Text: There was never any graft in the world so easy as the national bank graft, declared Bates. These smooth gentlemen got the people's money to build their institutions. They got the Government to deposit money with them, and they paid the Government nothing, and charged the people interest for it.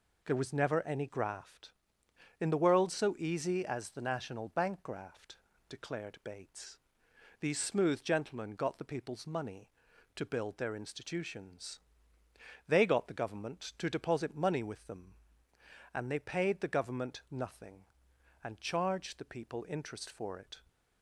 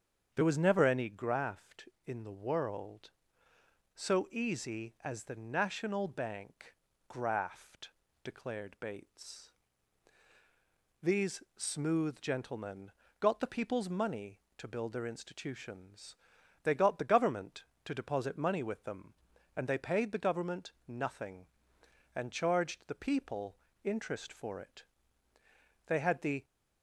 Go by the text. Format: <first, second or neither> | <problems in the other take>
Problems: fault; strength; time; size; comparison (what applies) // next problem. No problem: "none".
first | starts louder than the rest; strong; until 1.3 s; 7.5 dB // pauses between "bank" and "graft"; slight; at 6.7 s; 0.34 s long // pauses between "gentlemen" and "got"; slight; at 12.9 s; 0.28 s long // pauses between "Government" and "nothing"; slight; at 20.7 s; 0.16 s long // pauses between "people" and "interest"; slight; at 23.5 s; 0.28 s long // goes on to say "They had the"; from 25.8 s on; 0.56 s long